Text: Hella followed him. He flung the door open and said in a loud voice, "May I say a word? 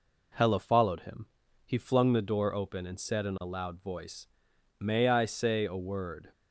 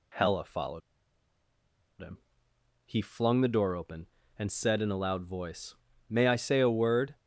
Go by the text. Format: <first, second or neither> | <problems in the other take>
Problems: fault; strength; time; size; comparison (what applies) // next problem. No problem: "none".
first | pauses between "followed" and "him"; at 0.8 s; 1.2 s long